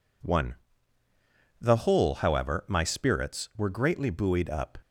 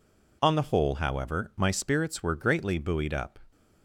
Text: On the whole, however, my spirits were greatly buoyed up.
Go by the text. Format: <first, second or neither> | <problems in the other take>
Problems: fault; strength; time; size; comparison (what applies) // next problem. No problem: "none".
second | says "One" for "On"; at 0.2 s